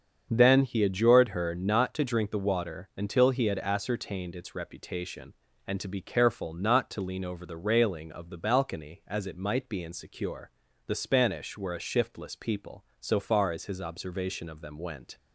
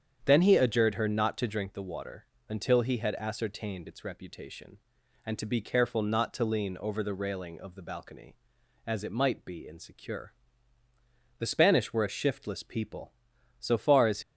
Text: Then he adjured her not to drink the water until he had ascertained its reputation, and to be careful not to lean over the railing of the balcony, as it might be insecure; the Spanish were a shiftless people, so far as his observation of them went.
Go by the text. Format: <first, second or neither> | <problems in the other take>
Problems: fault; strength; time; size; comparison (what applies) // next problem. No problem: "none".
first | starts louder than the rest; strong; until 1.2 s; 8 dB; also in the first // pauses between "water" and "until"; slight; at 2.2 s; 0.22 s long // stops before "his observation of them went"; at 14.2 s